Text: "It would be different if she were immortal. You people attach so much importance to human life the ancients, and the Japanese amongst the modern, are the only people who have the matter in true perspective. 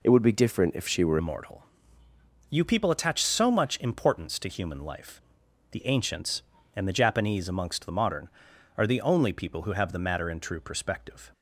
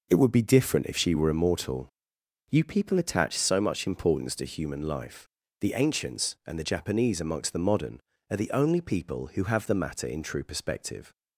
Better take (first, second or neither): second